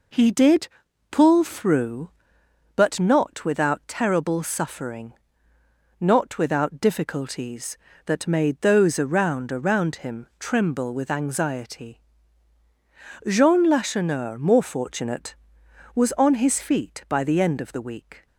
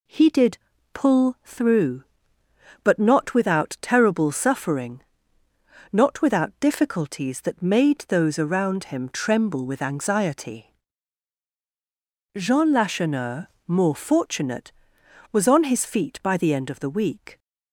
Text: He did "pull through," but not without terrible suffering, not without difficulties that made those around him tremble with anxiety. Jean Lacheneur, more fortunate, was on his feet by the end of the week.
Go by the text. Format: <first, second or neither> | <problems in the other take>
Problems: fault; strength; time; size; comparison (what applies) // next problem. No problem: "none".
second | pauses between "did" and "pull"; at 0.6 s; 0.42 s long; slight in the second // says "around" twice; at 9.5 s